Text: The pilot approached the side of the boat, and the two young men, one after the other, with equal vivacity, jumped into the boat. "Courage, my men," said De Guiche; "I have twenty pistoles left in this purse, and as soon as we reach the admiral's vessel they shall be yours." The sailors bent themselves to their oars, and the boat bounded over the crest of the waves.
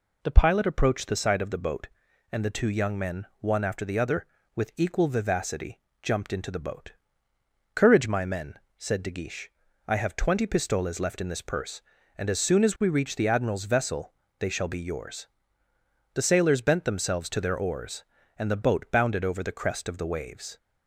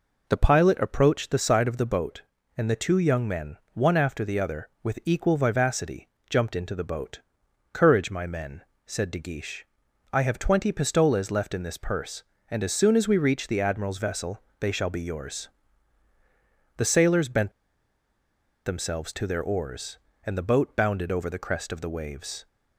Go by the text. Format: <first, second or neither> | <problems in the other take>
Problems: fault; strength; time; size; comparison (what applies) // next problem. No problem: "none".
first | pauses between "vessel" and "they"; slight; at 14.4 s; 0.20 s long; slight in the first // pauses between "bent" and "themselves"; at 17.5 s; 1.1 s long